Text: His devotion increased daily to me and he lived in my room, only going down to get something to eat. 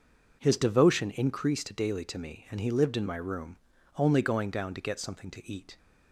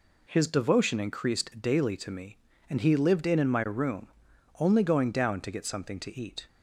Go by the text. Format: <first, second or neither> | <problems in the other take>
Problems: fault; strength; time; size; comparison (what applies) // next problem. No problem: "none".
first | says "in" twice; at 3.3 s